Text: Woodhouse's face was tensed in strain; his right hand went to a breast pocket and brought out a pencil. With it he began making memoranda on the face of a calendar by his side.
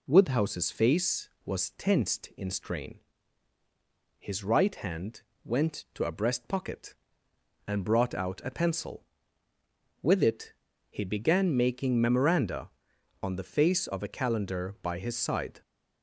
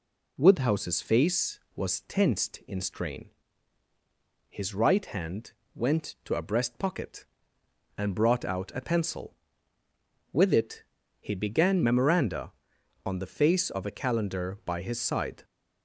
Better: first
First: pauses between "hand" and "went"; slight; at 5.2 s; 0.22 s long // pauses between "it" and "he"; slight; at 10.5 s; 0.36 s long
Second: pauses between "hand" and "went"; slight; at 5.5 s; 0.22 s long // pauses between "it" and "he"; slight; at 10.8 s; 0.36 s long // skips "making"; at 11.8 s

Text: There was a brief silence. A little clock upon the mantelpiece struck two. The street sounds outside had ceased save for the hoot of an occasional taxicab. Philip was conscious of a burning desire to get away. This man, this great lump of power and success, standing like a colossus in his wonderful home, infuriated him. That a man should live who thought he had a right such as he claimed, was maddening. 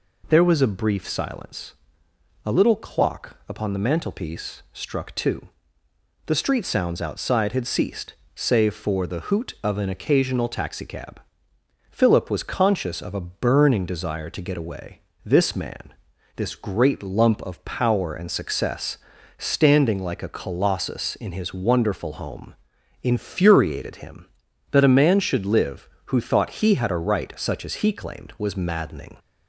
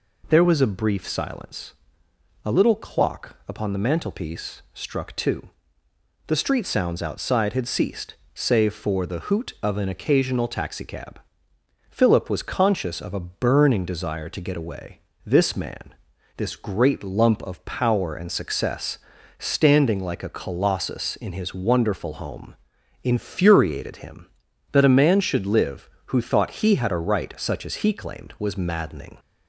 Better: neither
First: pauses between "ceased" and "save"; slight; at 8.1 s; 0.22 s long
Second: pauses between "ceased" and "save"; slight; at 8.1 s; 0.20 s long

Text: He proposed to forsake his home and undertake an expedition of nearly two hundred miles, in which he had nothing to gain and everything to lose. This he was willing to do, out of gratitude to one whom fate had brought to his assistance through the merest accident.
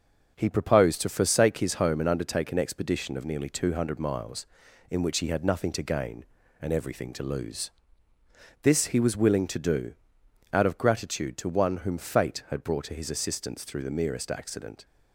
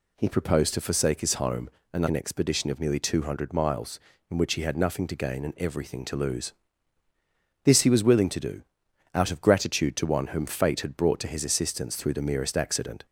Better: first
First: none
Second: skips "undertake"; at 2.0 s

